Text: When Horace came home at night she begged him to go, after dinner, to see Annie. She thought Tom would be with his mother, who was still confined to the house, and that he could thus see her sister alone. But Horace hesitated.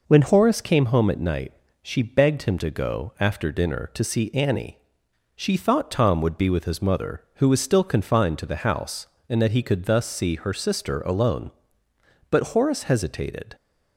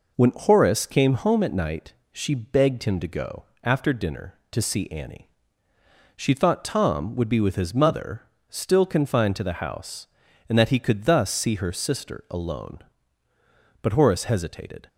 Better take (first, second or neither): first